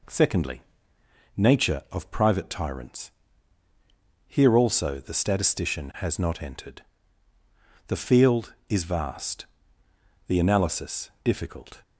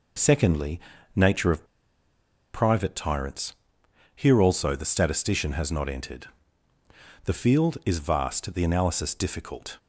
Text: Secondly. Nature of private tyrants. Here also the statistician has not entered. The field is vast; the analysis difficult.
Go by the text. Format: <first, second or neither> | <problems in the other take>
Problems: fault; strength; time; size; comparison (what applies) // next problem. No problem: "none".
first | pauses between "of" and "private"; noticeable; at 1.6 s; 0.88 s long